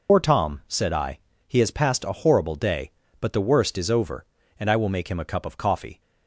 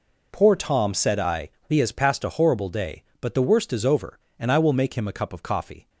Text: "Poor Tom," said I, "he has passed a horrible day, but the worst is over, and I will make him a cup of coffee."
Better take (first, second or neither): second